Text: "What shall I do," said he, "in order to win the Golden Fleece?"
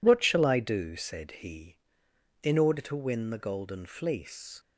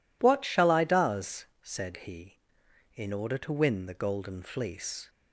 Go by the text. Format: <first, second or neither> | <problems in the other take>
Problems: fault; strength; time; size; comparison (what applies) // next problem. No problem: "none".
first | says "does" for "do"; at 0.8 s